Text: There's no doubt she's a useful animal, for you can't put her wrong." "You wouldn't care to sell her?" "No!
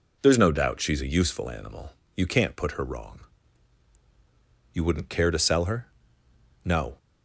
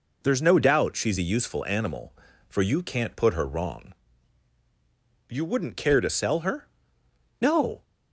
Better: second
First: skips "for"; at 2.0 s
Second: none

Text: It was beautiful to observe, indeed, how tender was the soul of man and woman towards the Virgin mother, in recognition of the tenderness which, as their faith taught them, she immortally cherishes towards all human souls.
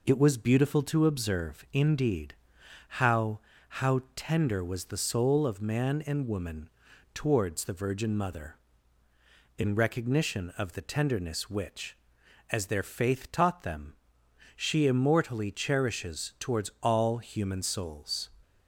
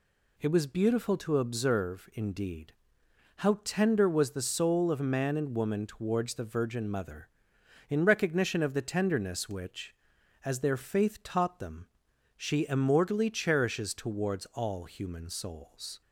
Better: second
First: says "how" twice; at 3.8 s // pauses between "woman" and "towards"; noticeable; at 6.6 s; 0.46 s long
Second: none

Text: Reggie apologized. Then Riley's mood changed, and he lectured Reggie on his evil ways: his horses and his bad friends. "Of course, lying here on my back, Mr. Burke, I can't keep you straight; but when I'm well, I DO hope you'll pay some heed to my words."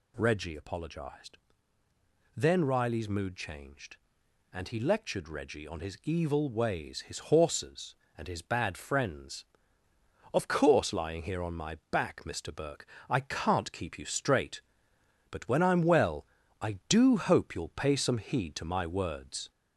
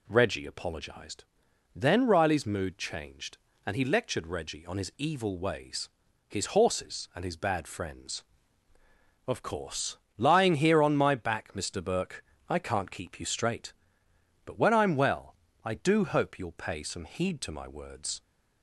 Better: second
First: gets louder; throughout; 3.5 dB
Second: none

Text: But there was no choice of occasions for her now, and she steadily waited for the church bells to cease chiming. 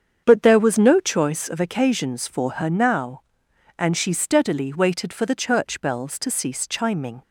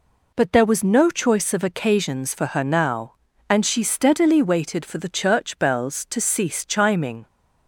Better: second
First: starts louder than the rest; strong; until 1.2 s; 7 dB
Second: none

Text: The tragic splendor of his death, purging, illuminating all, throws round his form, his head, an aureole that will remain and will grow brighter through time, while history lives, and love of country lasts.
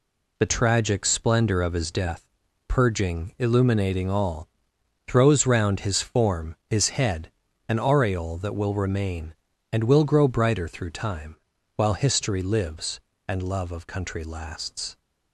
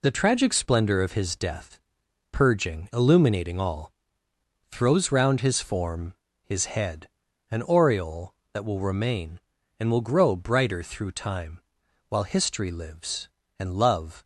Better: first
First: none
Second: stops before "of country lasts"; at 14.2 s

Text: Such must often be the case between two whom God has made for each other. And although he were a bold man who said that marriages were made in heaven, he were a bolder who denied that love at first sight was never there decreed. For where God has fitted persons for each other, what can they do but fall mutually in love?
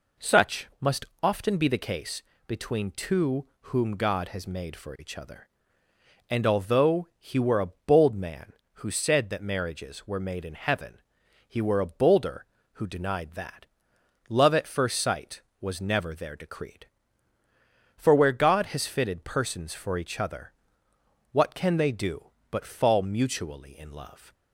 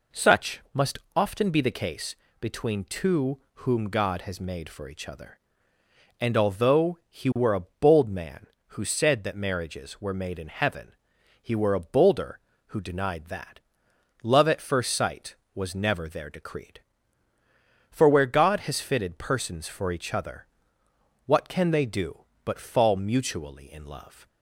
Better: neither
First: pauses between "must" and "often"; slight; at 1.0 s; 0.18 s long // pauses between "case" and "between"; slight; at 2.2 s; 0.24 s long // pauses between "two" and "whom"; slight; at 3.4 s; 0.16 s long // pauses between "that" and "love"; noticeable; at 13.6 s; 0.64 s long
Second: pauses between "must" and "often"; slight; at 0.9 s; 0.18 s long // pauses between "case" and "between"; slight; at 2.1 s; 0.24 s long // pauses between "two" and "whom"; slight; at 3.3 s; 0.16 s long // pauses between "that" and "love"; noticeable; at 13.5 s; 0.64 s long

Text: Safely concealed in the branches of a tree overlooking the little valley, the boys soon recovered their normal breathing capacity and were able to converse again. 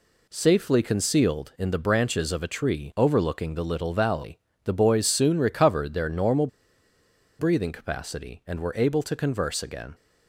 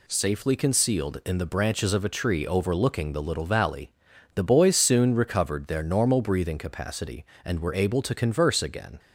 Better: second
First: pauses between "normal" and "breathing"; noticeable; at 6.4 s; 0.91 s long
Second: none

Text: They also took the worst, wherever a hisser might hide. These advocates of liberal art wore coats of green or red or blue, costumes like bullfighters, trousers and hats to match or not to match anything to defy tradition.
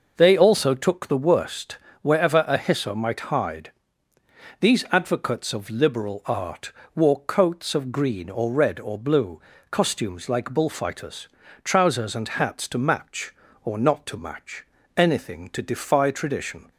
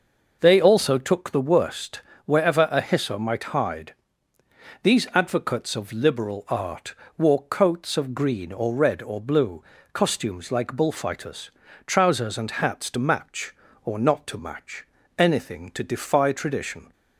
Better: neither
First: pauses between "art" and "wore"; slight; at 6.7 s; 0.24 s long // pauses between "match" and "anything"; slight; at 14.6 s; 0.33 s long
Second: pauses between "art" and "wore"; slight; at 6.9 s; 0.24 s long // pauses between "match" and "anything"; slight; at 14.8 s; 0.34 s long

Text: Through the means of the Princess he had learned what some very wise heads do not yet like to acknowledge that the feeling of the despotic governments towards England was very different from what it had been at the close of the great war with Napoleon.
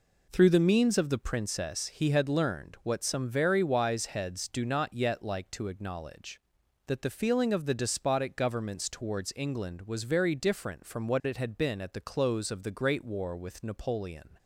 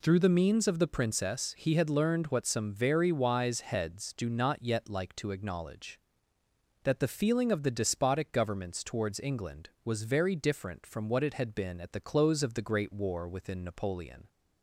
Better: first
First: none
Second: says "within" for "with"; at 13.2 s

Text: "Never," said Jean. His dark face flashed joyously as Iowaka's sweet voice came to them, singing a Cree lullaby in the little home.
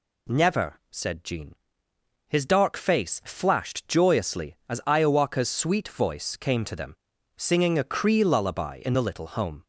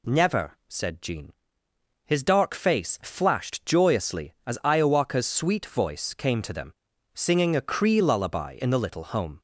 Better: neither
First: none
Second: none

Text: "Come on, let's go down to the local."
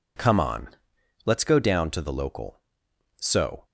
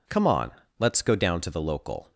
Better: second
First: goes on to say "So"; slight; from 3.1 s on; 0.48 s long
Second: none

